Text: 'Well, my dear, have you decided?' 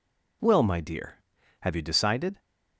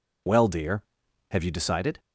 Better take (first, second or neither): first